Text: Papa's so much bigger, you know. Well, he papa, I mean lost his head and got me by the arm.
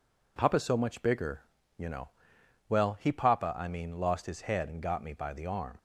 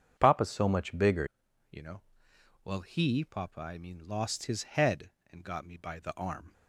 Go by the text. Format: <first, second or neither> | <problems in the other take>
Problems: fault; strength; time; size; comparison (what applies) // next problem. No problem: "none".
first | starts louder than the rest; strong; until 1.1 s; 7.5 dB // changes voice at "you"; from 1.7 s on; 4.8 s long